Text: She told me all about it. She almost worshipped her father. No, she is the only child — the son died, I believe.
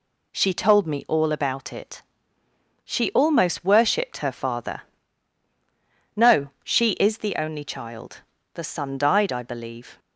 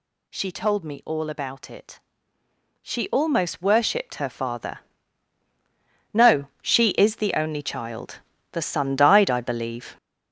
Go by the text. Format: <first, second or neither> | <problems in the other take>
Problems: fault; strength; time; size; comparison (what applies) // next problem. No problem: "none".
first | gets louder; throughout; 7 dB